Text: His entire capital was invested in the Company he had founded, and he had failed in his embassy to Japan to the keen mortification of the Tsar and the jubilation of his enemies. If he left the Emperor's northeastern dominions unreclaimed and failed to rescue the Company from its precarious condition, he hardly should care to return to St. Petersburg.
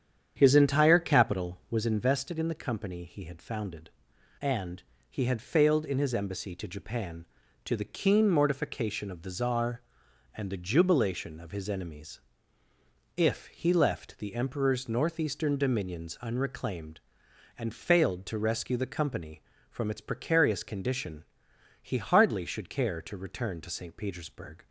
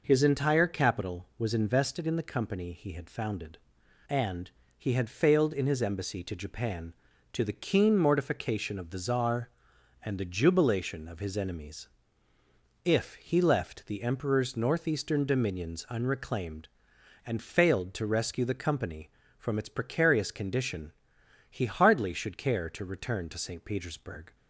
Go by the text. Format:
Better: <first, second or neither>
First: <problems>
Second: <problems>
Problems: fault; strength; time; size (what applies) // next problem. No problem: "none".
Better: second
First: starts louder than the rest; strong; until 1.9 s; 8.5 dB // pauses between "and" and "he"; slight; at 4.8 s; 0.26 s long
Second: pauses between "and" and "he"; slight; at 4.5 s; 0.26 s long